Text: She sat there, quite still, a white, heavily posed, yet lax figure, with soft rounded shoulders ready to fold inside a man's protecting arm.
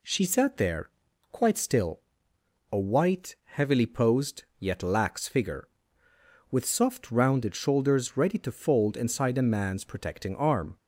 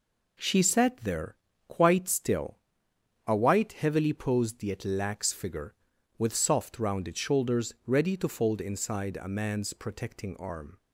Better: neither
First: none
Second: none

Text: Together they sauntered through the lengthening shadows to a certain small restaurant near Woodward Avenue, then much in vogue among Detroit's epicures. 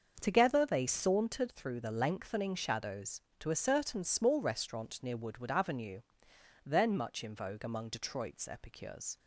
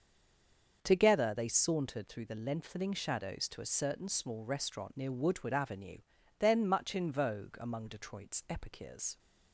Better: first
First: starts louder than the rest; until 1.2 s; 6.5 dB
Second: stays silent before the first word; slight; until 0.8 s; 0.8 s long // starts louder than the rest; until 1.8 s; 6.5 dB

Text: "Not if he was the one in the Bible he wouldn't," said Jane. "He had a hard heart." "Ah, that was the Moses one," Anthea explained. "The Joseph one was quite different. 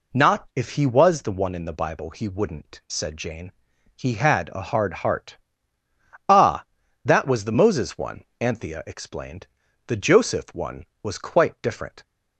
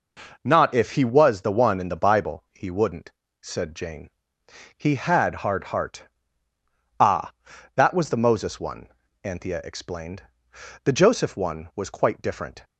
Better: first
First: none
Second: skips "a"; at 5.4 s

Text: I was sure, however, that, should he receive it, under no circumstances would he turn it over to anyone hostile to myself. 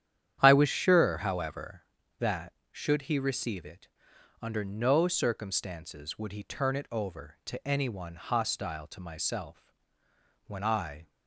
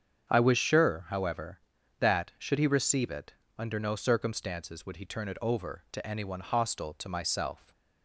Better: second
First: starts louder than the rest; strong; until 1.4 s; 9.5 dB // goes on to say "When I"; noticeable; from 10.4 s on; 0.62 s long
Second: starts louder than the rest; strong; until 1.3 s; 7.5 dB

